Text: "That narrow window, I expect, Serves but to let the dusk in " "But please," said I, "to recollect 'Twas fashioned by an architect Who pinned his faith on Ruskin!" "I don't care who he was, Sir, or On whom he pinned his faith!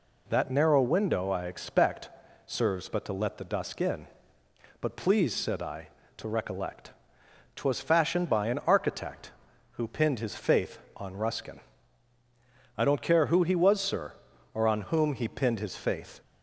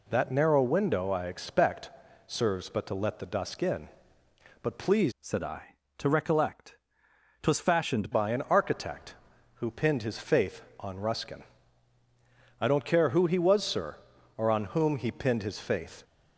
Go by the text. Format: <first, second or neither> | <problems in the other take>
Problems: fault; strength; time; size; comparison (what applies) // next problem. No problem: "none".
first | changes voice from "said" to "fashioned"; from 5.1 to 8.1 s; 3.0 s long // pauses between "recollect" and "Twas"; noticeable; at 6.7 s; 0.64 s long; noticeable in the first